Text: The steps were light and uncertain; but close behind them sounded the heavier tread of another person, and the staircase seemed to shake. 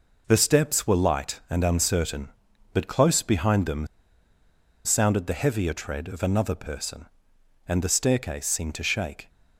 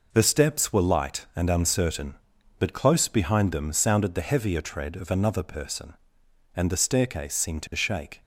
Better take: second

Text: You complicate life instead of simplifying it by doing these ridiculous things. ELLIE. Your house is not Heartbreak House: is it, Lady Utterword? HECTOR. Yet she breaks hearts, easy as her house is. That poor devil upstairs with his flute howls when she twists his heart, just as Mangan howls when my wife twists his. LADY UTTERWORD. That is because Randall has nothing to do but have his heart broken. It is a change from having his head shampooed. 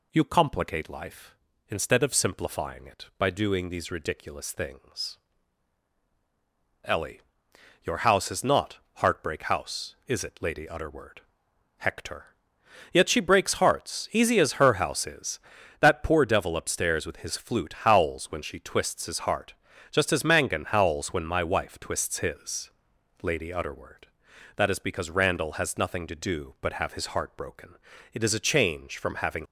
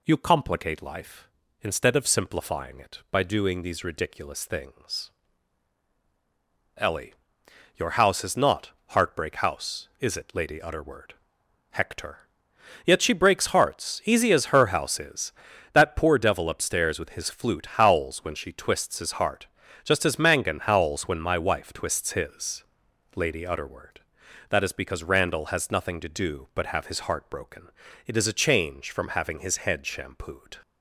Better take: second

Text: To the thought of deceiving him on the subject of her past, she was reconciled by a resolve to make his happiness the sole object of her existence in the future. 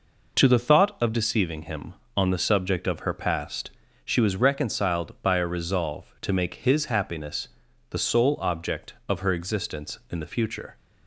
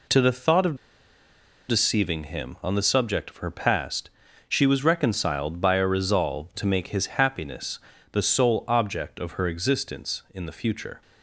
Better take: first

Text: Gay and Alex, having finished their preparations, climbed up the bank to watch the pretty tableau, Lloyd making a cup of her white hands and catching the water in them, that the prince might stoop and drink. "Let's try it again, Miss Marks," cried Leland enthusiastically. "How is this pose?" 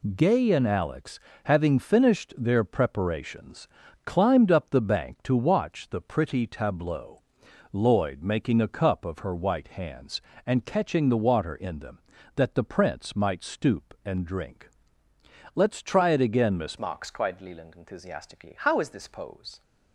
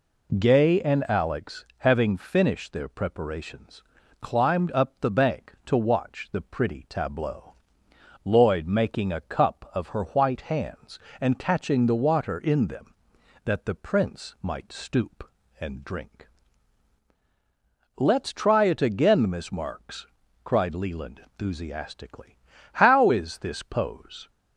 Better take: second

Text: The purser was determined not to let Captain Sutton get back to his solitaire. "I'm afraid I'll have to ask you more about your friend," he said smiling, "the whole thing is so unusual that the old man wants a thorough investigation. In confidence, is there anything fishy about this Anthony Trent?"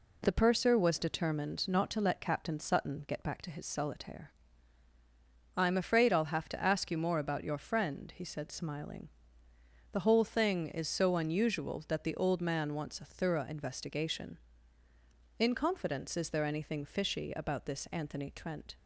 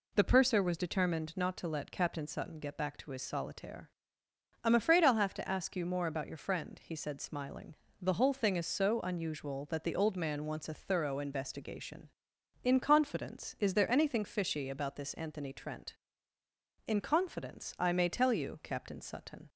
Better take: first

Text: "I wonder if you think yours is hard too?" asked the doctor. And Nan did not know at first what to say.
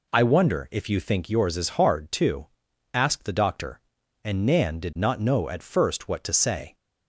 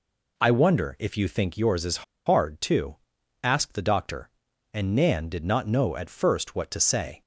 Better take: first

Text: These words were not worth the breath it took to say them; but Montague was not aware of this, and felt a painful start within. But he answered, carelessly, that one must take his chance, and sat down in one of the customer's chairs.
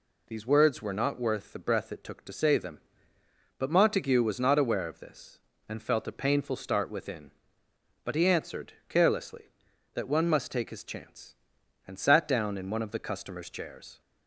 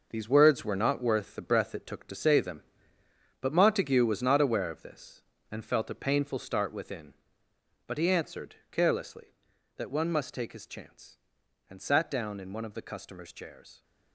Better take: first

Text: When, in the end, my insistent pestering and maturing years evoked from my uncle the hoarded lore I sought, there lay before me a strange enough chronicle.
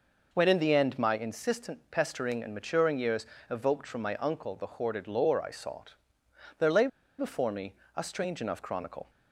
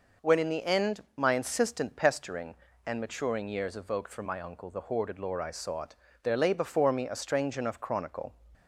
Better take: second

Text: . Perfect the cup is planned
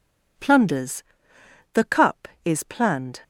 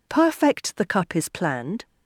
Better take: second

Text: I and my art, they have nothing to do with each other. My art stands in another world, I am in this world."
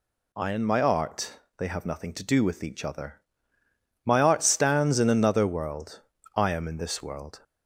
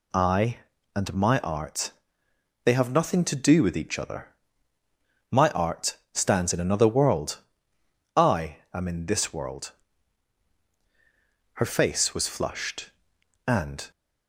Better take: first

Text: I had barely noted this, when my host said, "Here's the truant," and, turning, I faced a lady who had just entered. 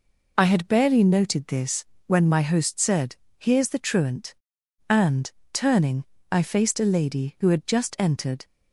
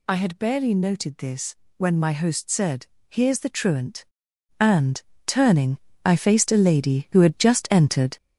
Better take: first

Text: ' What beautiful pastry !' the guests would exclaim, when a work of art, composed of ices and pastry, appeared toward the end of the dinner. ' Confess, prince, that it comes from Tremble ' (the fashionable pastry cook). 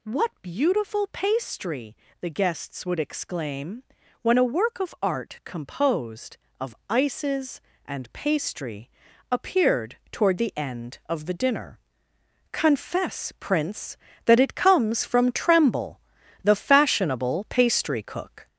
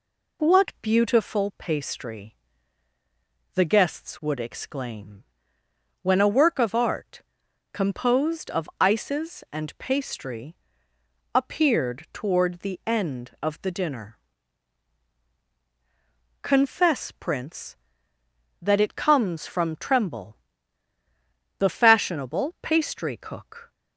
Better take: second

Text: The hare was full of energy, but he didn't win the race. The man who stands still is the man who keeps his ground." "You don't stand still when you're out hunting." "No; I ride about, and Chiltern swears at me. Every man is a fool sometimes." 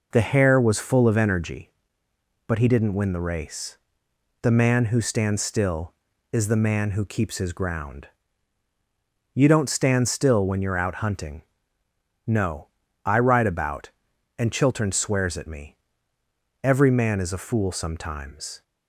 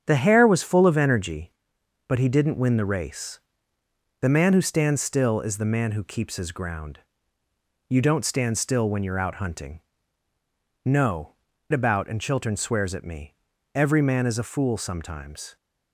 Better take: first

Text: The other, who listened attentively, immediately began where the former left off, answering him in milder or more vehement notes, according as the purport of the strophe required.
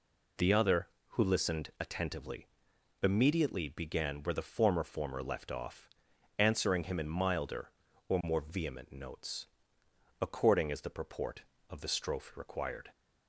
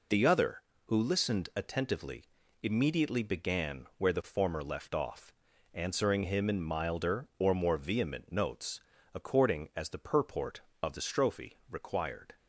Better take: second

